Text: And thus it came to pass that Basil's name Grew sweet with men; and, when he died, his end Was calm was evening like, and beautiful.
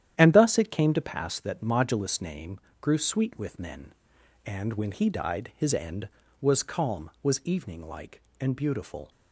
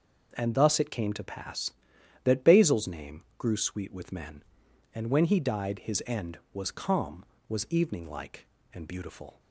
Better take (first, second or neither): second